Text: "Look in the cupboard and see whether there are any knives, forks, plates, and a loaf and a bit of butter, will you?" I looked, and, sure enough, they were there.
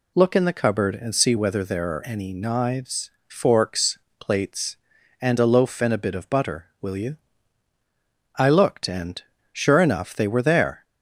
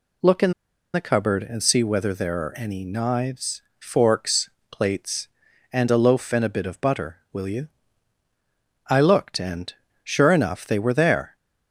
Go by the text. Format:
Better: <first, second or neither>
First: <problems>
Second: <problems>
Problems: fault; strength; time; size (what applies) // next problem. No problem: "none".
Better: first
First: none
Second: pauses between "in" and "the"; at 0.5 s; 0.41 s long